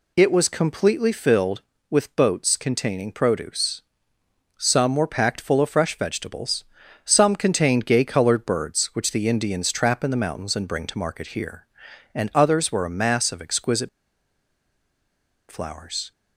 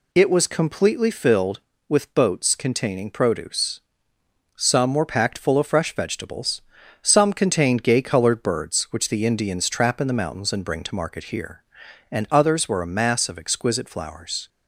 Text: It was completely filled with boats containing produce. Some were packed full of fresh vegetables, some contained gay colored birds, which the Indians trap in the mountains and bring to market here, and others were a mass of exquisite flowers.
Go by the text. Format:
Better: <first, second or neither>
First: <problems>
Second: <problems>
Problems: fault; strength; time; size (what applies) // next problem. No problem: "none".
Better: second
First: pauses between "exquisite" and "flowers"; strong; at 13.8 s; 1.6 s long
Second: none